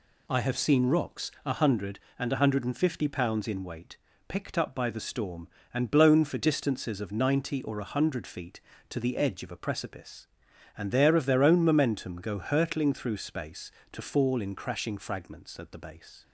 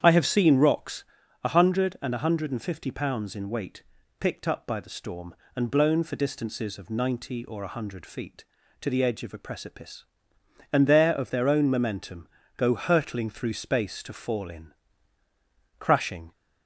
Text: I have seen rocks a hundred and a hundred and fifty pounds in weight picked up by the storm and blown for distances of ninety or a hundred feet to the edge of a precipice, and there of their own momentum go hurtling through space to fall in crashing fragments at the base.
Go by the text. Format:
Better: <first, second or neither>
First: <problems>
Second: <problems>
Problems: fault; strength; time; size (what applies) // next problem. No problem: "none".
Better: first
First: pauses between "weight" and "picked"; slight; at 3.9 s; 0.28 s long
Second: starts louder than the rest; strong; until 1.0 s; 8.5 dB // pauses between "rocks" and "a"; at 1.0 s; 0.40 s long // pauses between "weight" and "picked"; slight; at 3.8 s; 0.34 s long // pauses between "momentum" and "go"; slight; at 12.2 s; 0.30 s long // pauses between "in" and "crashing"; at 14.7 s; 1.0 s long // stops before "fragments at the base"; at 16.3 s